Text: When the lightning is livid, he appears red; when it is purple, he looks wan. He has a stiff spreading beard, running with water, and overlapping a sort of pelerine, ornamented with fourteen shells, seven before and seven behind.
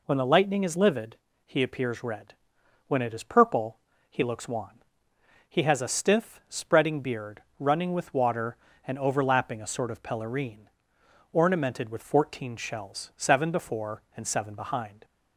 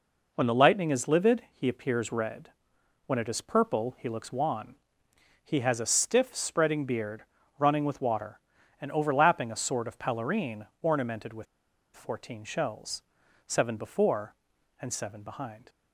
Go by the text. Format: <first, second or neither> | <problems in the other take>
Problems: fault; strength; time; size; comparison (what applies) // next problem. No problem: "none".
first | pauses between "with" and "fourteen"; noticeable; at 11.4 s; 0.49 s long